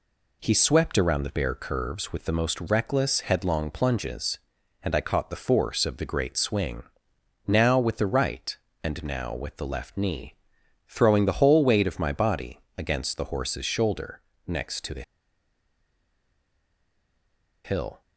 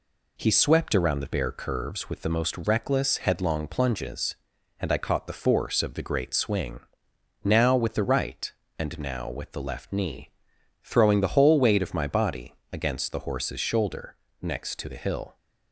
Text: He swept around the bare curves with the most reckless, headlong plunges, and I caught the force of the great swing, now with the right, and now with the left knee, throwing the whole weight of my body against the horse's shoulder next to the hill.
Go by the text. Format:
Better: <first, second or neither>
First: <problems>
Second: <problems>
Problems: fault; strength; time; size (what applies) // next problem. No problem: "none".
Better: second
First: pauses between "body" and "against"; slight; at 12.6 s; 0.16 s long // pauses between "shoulder" and "next"; slight; at 14.2 s; 0.26 s long // pauses between "the" and "hill"; strong; at 15.0 s; 2.6 s long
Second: pauses between "body" and "against"; slight; at 12.5 s; 0.16 s long // pauses between "shoulder" and "next"; slight; at 14.1 s; 0.26 s long